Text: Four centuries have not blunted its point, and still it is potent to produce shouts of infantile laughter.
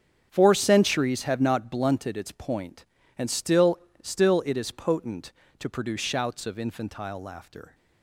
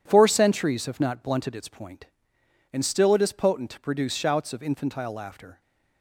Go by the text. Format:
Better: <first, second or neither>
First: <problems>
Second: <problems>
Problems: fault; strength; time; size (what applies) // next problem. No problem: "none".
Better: second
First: starts louder than the rest; strong; until 1.3 s; 8 dB // says "still" twice; at 4.0 s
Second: none